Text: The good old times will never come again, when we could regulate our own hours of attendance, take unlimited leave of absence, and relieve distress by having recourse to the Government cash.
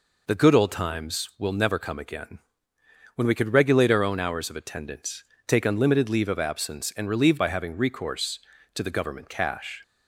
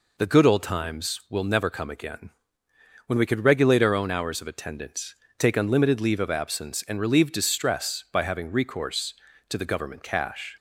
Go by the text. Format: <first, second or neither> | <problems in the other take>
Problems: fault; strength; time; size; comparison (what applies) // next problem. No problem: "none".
second | skips "distress"; at 7.3 s